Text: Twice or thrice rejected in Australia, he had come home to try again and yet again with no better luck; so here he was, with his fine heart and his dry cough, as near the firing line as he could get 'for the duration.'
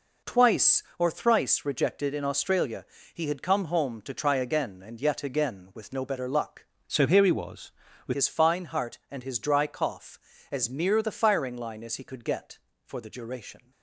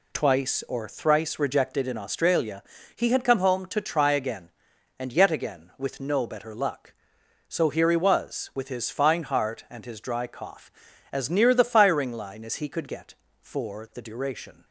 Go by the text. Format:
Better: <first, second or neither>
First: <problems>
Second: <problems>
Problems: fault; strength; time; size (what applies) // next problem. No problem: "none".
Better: second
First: changes voice from "so" to "with"; from 6.8 to 8.1 s; 1.3 s long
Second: none